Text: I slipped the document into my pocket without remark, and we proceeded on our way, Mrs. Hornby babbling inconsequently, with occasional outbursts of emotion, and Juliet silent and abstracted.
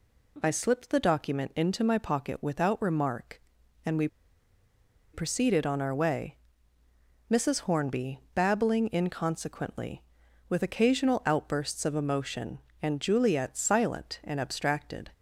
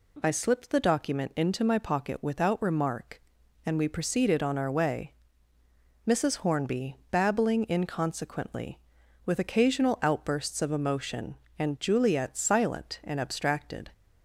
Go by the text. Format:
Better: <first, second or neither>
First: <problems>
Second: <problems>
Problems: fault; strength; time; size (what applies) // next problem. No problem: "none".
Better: second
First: pauses between "we" and "proceeded"; at 4.0 s; 1.0 s long // pauses between "Hornby" and "babbling"; slight; at 8.1 s; 0.16 s long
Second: pauses between "Hornby" and "babbling"; slight; at 6.9 s; 0.16 s long